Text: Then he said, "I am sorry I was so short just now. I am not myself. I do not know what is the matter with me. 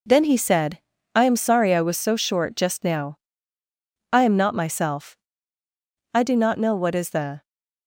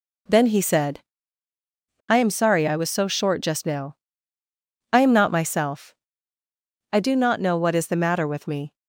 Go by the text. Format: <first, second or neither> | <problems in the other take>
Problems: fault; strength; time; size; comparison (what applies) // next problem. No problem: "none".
second | stops before "matter with me"; at 7.4 s